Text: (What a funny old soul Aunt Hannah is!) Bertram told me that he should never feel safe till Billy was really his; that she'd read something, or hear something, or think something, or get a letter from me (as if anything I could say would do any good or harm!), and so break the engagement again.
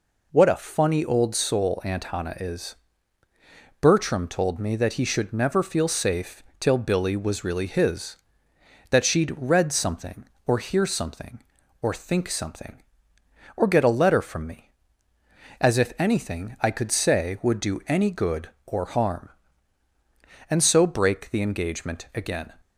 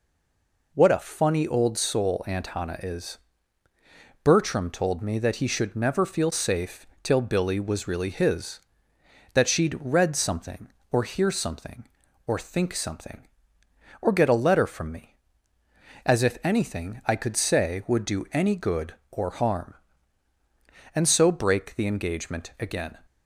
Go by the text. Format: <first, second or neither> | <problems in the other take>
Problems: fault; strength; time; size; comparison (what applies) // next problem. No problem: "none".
first | stays silent before the first word; slight; until 0.7 s; 0.7 s long // pauses between "safe" and "till"; slight; at 6.8 s; 0.16 s long; slight in the first